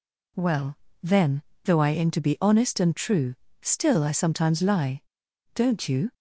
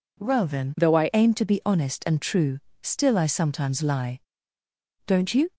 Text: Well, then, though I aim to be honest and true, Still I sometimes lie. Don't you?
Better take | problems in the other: first | changes voice from "though" to "I"; from 0.7 to 1.0 s; 0.3 s long

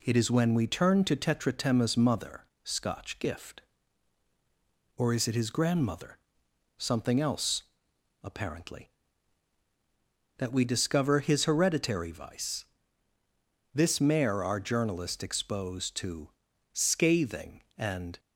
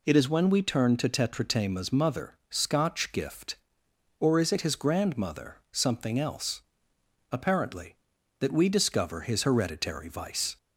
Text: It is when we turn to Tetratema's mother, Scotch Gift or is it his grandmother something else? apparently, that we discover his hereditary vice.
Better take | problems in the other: second | pauses between "grandmother" and "something"; noticeable; at 6.1 s; 0.60 s long // goes on to say "This mare our journalist exposed to scathing and"; strong; from 13.7 s on; 4.4 s long

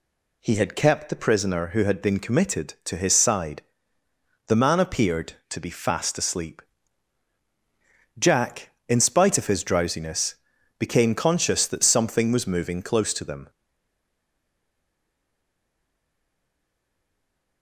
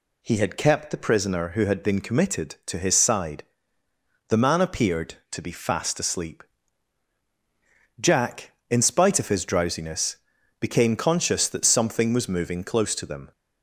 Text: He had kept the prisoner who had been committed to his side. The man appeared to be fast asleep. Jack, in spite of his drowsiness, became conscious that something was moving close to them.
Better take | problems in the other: second | stays silent after the last word; strong; from 13.4 s on; 4.2 s long

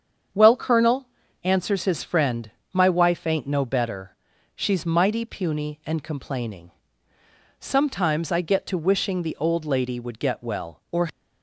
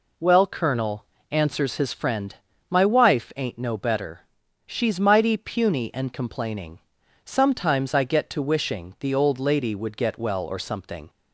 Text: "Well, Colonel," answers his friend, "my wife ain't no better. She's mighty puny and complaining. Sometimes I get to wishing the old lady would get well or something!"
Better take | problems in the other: second | starts louder than the rest; strong; until 1.6 s; 7.5 dB // stops before "something"; at 11.1 s

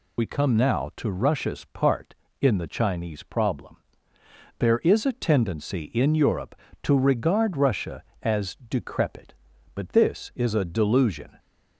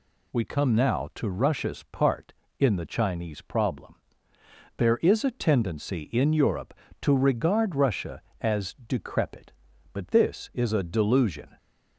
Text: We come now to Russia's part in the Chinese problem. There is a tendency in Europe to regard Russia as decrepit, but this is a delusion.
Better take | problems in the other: second | loses the start of "We"; at 0.1 s; 40 ms

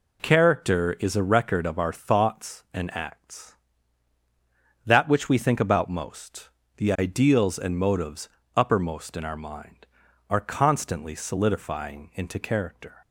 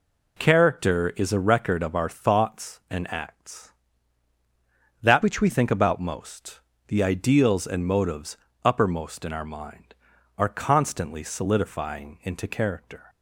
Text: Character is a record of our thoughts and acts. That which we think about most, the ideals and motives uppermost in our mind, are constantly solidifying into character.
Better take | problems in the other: first | changes voice from "which" to "we"; from 5.2 to 5.4 s; 0.2 s long // pauses between "motives" and "uppermost"; slight; at 8.3 s; 0.26 s long; slight in the first

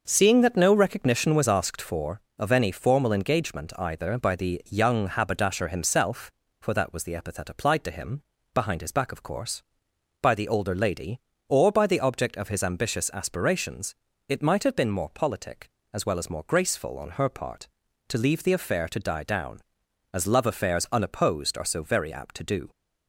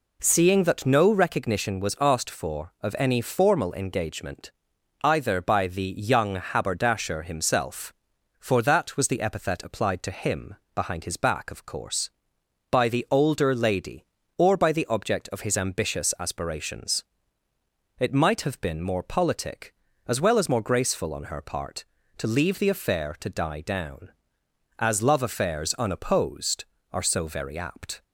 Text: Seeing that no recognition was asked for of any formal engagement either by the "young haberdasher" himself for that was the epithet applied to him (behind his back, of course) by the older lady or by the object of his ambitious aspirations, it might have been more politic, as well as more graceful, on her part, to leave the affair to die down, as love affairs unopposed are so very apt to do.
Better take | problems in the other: first | pauses between "engagement" and "either"; noticeable; at 4.5 s; 0.52 s long // stops before "to do"; at 28.0 s

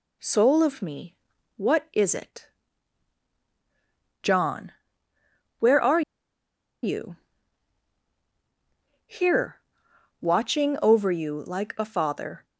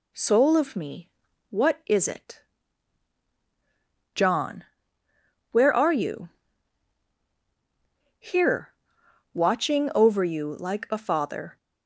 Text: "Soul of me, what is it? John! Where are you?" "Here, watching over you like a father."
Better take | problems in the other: second | pauses between "are" and "you"; noticeable; at 6.0 s; 0.82 s long

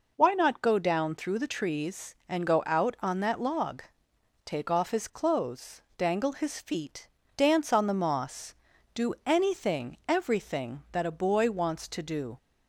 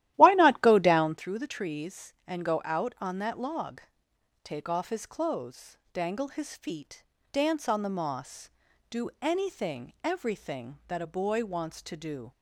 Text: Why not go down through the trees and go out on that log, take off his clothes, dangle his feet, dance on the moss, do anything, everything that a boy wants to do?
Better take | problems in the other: first | starts louder than the rest; strong; until 1.2 s; 14 dB

